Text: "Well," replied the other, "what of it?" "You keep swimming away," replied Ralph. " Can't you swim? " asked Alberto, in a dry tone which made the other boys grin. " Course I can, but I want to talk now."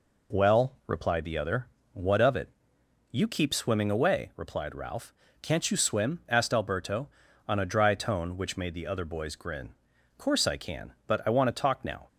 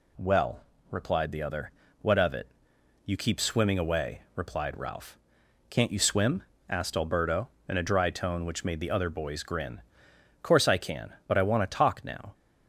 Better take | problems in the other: second | says "on" for "in"; at 7.4 s

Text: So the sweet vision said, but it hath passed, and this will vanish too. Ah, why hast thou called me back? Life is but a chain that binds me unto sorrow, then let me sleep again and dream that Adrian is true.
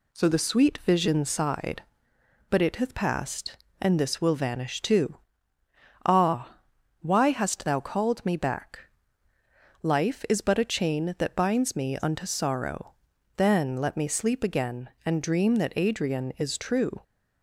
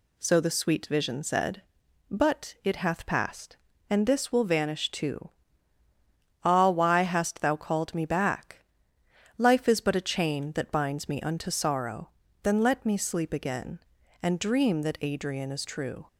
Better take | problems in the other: second | says "sighed" for "said"; at 1.2 s

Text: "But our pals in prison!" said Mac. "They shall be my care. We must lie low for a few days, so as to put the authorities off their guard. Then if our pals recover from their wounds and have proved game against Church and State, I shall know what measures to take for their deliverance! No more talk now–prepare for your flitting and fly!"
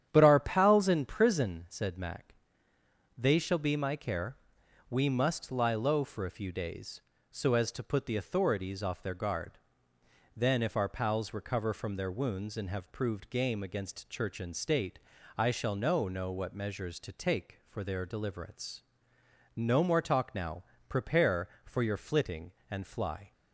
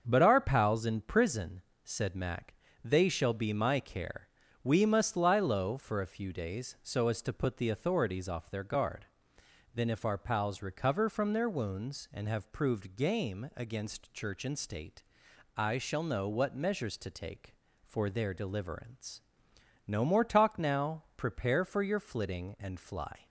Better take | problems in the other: second | starts louder than the rest; strong; until 1.1 s; 9.5 dB; also in the second // says "know" twice; at 16.0 s

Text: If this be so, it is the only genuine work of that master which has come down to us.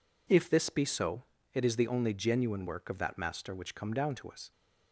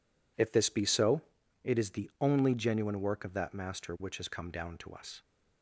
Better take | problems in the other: second | skips "has"; at 3.7 s

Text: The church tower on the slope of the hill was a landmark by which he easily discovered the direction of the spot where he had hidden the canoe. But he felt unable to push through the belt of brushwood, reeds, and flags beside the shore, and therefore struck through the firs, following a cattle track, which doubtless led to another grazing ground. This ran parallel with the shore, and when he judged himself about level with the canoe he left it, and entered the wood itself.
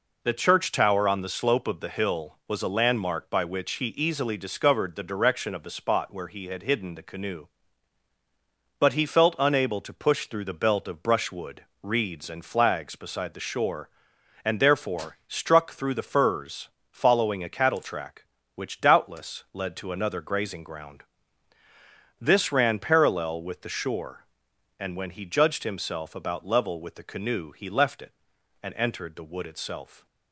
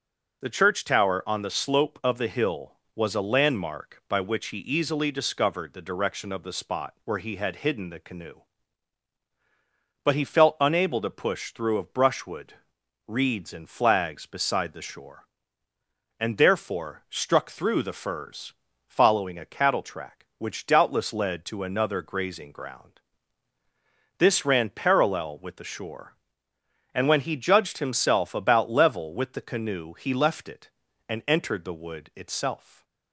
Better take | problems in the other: first | skips "the belt"; at 11.7 s // stays silent after the last word; slight; from 32.5 s on; 0.6 s long

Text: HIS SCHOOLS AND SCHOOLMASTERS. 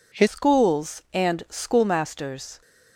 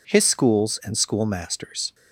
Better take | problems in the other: second | changes voice at "SCHOOLS"; from 0.2 s on; 2.4 s long

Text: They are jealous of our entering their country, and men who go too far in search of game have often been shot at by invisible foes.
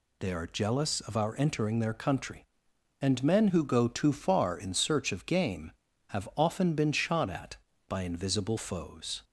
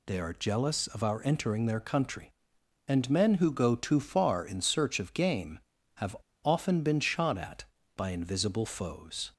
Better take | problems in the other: first | pauses between "have" and "often"; slight; at 6.1 s; 0.28 s long

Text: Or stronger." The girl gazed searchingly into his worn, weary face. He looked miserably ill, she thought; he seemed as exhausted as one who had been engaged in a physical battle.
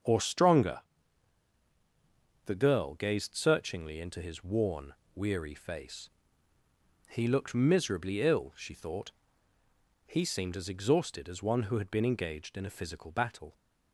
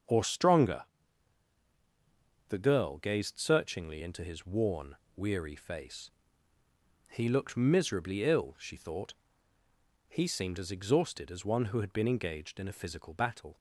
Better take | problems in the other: neither | starts louder than the rest; the same in both

